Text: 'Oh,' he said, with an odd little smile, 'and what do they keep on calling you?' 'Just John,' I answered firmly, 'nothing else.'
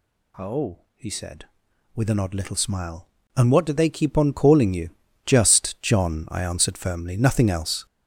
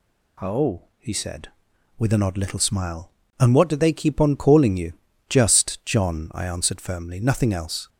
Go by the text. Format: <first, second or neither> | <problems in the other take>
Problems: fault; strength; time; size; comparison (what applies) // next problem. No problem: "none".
second | gets louder; strong; throughout; 8 dB